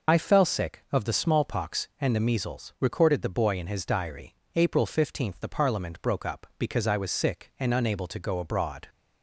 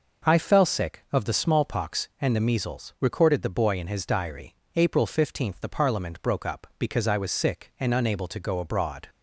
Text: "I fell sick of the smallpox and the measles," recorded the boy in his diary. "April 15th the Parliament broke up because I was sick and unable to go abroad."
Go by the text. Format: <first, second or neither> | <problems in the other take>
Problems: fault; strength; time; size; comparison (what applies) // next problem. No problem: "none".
second | loses the start of "I"; at 0.0 s; 60 ms